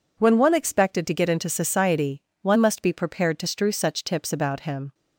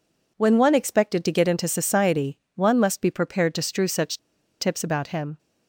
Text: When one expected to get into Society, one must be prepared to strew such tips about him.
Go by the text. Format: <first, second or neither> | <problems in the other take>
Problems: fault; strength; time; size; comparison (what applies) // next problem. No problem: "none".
first | pauses between "such" and "tips"; at 4.1 s; 0.42 s long